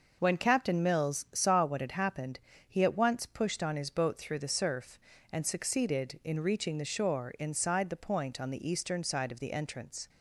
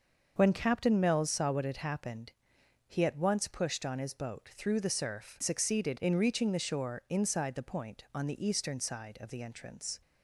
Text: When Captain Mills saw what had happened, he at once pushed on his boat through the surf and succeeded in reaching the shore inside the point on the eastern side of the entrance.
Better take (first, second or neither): first